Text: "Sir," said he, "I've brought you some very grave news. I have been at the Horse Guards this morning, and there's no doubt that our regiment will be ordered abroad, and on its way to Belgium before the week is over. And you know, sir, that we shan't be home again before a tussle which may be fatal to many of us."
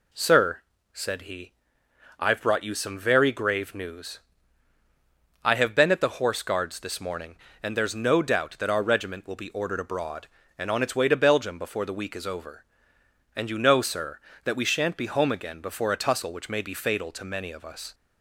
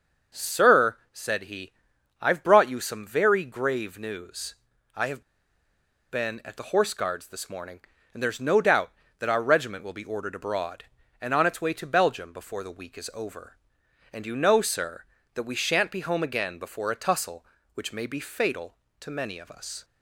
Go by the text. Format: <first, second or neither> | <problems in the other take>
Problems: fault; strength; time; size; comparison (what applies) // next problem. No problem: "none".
first | starts louder than the rest; until 1.4 s; 6.5 dB // pauses between "have" and "been"; noticeable; at 5.2 s; 0.89 s long